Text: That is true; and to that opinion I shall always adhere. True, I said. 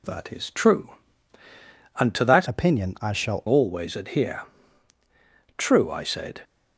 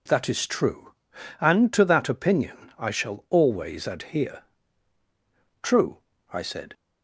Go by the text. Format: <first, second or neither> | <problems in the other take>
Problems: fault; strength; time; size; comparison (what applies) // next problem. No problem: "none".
second | changes voice from "opinion" to "shall"; from 2.4 to 3.4 s; 1.0 s long